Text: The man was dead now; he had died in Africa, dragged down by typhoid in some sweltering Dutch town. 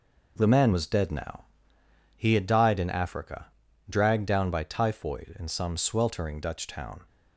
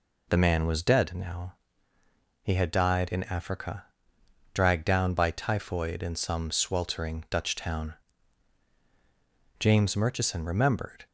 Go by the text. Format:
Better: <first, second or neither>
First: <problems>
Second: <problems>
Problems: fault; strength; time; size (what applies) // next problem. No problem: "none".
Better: first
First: none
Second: goes on to say "James Murchison remembered"; from 9.5 s on; 1.4 s long